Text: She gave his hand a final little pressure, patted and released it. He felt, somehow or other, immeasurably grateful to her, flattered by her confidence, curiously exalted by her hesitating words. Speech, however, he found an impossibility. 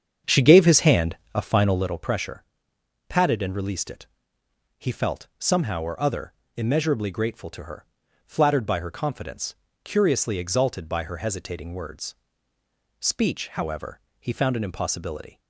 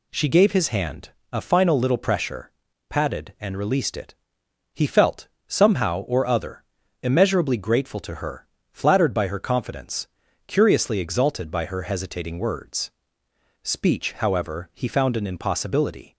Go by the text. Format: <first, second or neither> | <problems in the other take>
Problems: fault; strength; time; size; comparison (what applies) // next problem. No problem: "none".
second | starts louder than the rest; strong; until 1.9 s; 7.5 dB // pauses between "hand" and "a"; slight; at 1.1 s; 0.18 s long; slight in the second